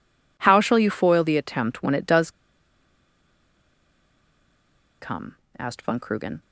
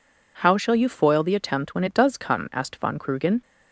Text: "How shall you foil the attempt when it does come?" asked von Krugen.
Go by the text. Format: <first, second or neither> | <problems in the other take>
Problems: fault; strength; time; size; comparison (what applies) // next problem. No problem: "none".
second | pauses between "does" and "come"; strong; at 2.2 s; 2.7 s long